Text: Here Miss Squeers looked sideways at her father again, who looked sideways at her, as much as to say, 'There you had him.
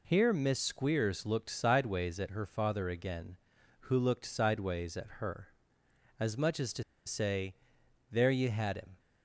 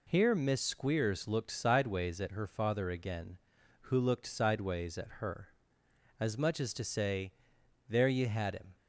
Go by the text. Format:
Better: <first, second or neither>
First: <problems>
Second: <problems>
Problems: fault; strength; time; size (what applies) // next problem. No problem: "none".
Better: second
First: pauses between "to" and "say"; slight; at 6.8 s; 0.23 s long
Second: none